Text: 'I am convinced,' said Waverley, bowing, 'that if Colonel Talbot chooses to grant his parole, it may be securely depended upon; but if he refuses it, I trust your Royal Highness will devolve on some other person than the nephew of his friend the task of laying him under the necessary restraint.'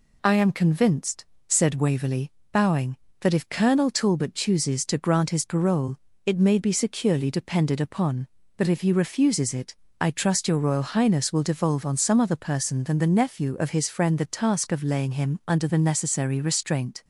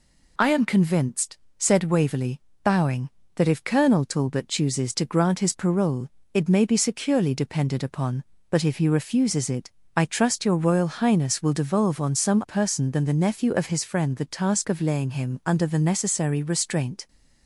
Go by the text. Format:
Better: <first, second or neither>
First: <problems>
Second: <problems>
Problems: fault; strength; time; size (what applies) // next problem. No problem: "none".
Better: first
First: none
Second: skips "other"; at 12.4 s